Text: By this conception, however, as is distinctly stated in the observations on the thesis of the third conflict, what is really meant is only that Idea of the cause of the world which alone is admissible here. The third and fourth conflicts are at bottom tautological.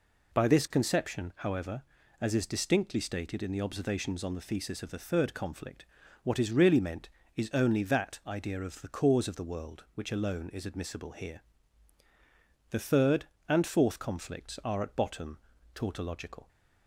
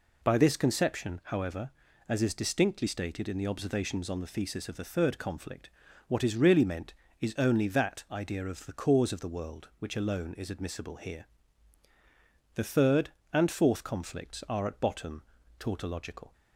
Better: neither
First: pauses between "bottom" and "tautological"; slight; at 15.3 s; 0.36 s long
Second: pauses between "bottom" and "tautological"; slight; at 15.2 s; 0.36 s long

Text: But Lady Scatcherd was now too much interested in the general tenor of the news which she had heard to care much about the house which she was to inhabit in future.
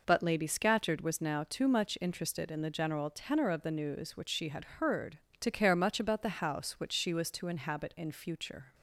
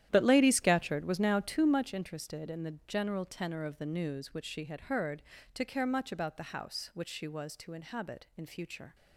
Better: first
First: none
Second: starts louder than the rest; strong; until 1.8 s; 11.5 dB

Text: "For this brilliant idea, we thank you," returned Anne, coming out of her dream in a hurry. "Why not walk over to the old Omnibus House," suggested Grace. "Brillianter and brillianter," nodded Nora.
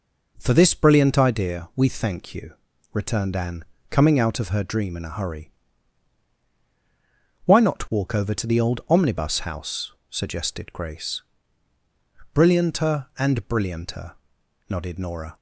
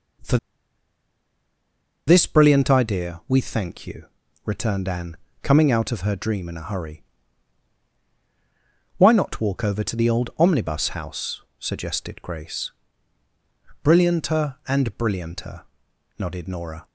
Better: first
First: none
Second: pauses between "For" and "this"; strong; at 0.3 s; 1.6 s long

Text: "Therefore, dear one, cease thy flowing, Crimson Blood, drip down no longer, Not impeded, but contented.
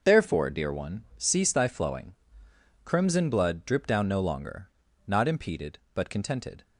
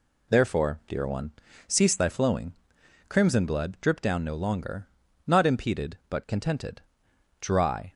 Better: first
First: none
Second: goes on to say "Dry"; from 7.3 s on; 0.54 s long

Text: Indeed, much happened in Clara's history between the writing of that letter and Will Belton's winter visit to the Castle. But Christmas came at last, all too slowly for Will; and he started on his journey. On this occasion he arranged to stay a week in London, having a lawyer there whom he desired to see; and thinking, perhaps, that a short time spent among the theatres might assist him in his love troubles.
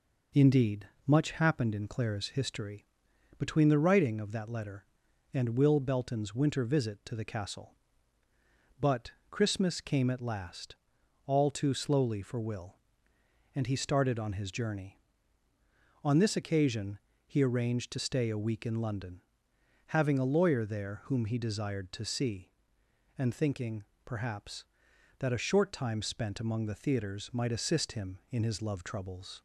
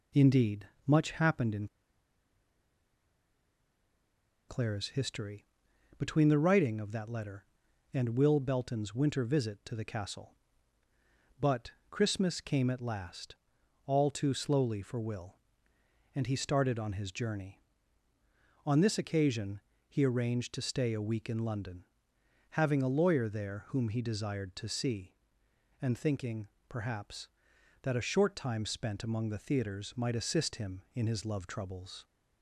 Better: first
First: pauses between "history" and "between"; noticeable; at 2.8 s; 0.52 s long // pauses between "But" and "Christmas"; slight; at 9.1 s; 0.18 s long // pauses between "occasion" and "he"; slight; at 16.9 s; 0.28 s long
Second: pauses between "in" and "Clara's"; strong; at 1.6 s; 2.8 s long // pauses between "history" and "between"; noticeable; at 5.4 s; 0.52 s long // pauses between "But" and "Christmas"; slight; at 11.7 s; 0.18 s long // pauses between "occasion" and "he"; slight; at 19.6 s; 0.28 s long

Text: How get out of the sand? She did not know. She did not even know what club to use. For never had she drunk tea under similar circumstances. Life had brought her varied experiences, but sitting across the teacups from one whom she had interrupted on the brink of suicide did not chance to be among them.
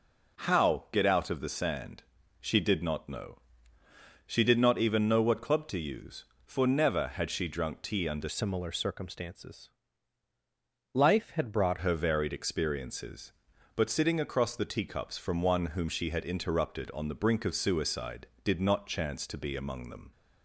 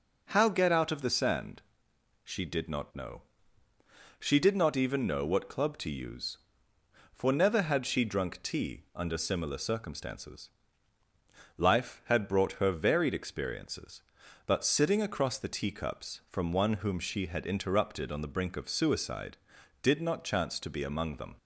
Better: second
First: changes voice from "similar" to "brought"; from 8.2 to 11.7 s; 3.5 s long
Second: none

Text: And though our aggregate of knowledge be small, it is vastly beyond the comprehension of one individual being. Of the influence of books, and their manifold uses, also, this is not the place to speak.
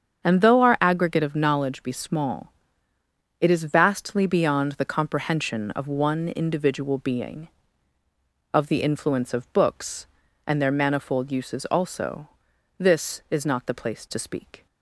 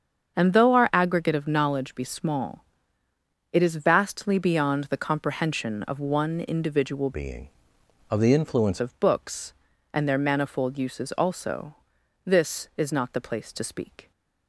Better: first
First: starts louder than the rest; strong; until 1.2 s; 7.5 dB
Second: starts louder than the rest; strong; until 1.4 s; 7 dB // changes voice from "being" to "influence"; from 7.1 to 8.7 s; 1.6 s long

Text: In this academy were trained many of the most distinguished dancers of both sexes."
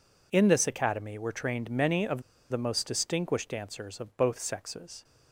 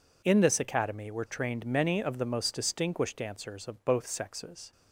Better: second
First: pauses between "of" and "the"; slight; at 2.2 s; 0.28 s long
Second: none

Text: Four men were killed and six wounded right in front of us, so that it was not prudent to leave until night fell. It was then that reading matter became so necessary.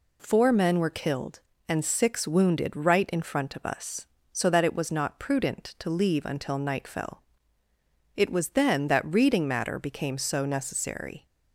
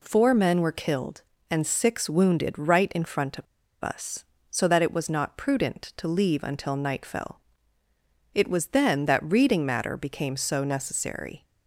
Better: first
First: none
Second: pauses between "of" and "us"; at 3.4 s; 0.38 s long

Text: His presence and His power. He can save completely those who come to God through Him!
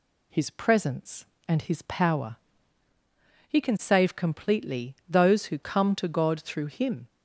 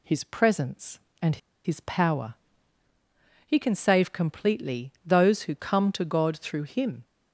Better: first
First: none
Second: pauses between "and" and "His"; slight; at 1.3 s; 0.29 s long

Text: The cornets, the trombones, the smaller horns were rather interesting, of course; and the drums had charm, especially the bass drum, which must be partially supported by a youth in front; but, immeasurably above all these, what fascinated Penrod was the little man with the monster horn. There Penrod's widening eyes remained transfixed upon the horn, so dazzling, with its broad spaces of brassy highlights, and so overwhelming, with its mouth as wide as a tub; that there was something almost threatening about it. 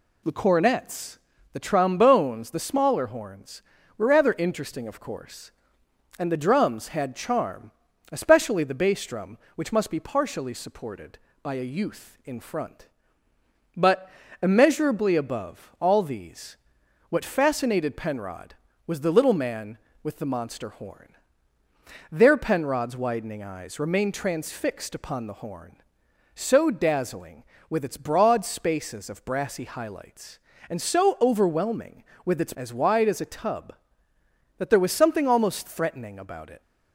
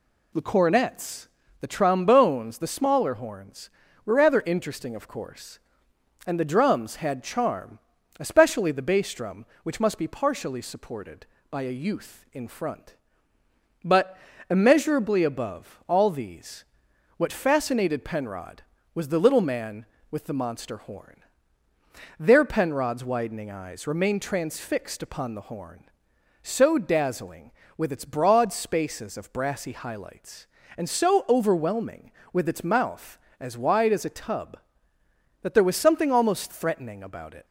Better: second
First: skips "mouth"; at 32.5 s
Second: none

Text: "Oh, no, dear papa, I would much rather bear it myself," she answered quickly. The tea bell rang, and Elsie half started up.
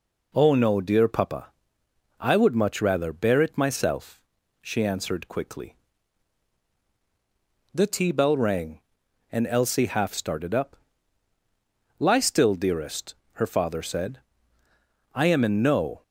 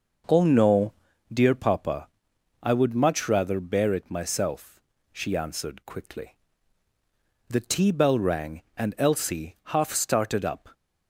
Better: second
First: goes on to say "Lie still dearest her father said I am in no"; strong; from 11.9 s on; 4.0 s long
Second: none

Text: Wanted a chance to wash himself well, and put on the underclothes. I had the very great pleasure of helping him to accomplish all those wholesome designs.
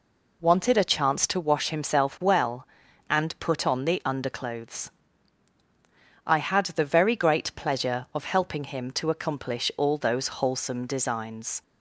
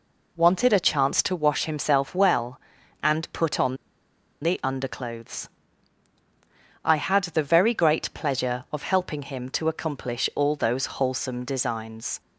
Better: first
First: none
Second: pauses between "on" and "the"; noticeable; at 3.7 s; 0.67 s long

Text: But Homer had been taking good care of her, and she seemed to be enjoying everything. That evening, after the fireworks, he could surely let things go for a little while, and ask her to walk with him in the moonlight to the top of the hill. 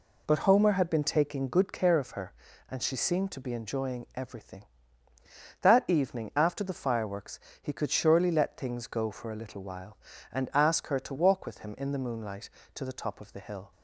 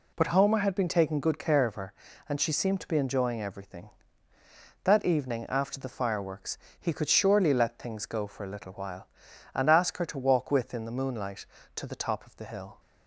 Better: first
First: none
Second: skips "him"; at 10.7 s

